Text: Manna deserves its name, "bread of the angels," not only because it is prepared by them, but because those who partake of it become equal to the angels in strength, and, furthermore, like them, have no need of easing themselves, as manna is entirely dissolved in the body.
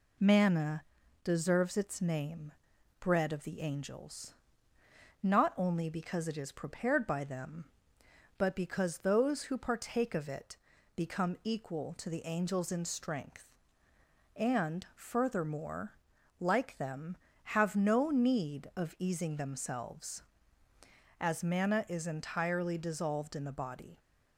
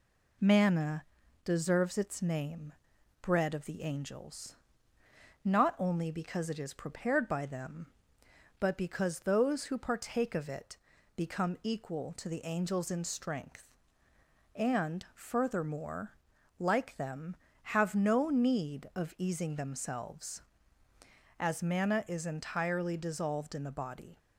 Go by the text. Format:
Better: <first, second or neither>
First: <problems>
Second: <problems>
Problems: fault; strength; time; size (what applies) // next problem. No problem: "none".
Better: neither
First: pauses between "Manna" and "deserves"; at 0.8 s; 0.38 s long // pauses between "it" and "become"; at 10.5 s; 0.38 s long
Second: pauses between "Manna" and "deserves"; at 1.0 s; 0.38 s long // pauses between "it" and "become"; at 10.7 s; 0.38 s long